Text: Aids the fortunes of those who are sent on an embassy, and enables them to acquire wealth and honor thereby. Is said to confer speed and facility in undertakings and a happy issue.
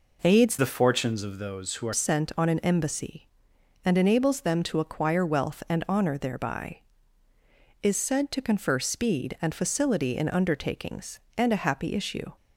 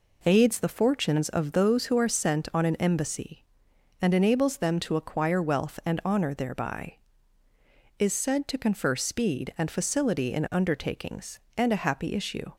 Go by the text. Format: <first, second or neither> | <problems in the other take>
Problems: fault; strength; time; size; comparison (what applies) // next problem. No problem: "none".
second | changes voice from "the" to "are"; from 0.5 to 1.9 s; 1.4 s long